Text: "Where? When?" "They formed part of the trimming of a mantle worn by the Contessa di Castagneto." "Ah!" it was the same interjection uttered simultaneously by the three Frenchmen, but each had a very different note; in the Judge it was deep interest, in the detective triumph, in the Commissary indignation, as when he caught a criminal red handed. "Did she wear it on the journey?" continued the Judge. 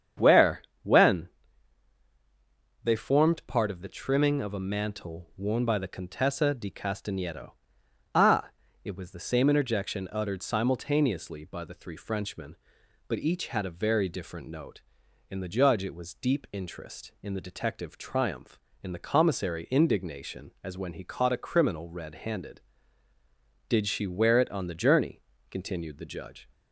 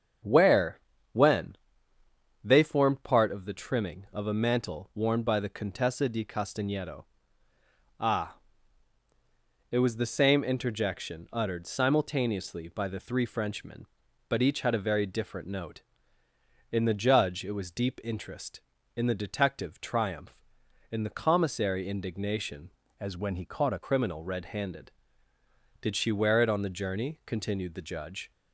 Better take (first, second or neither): first